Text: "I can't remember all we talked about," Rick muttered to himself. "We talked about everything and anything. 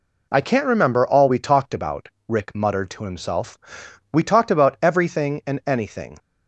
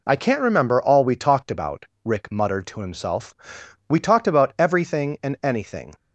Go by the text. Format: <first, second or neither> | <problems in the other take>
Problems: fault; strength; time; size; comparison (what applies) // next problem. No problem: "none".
neither | none